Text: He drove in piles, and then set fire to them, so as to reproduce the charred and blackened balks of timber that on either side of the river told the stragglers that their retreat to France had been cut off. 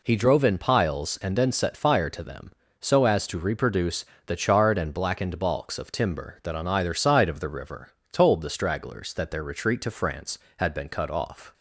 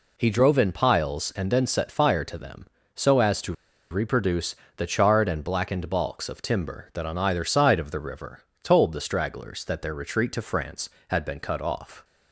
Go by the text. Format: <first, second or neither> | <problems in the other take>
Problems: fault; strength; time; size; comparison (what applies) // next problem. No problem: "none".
first | pauses between "to" and "reproduce"; at 3.5 s; 0.38 s long // pauses between "reproduce" and "the"; slight; at 4.5 s; 0.22 s long; slight in the first // pauses between "river" and "told"; slight; at 8.3 s; 0.22 s long; slight in the first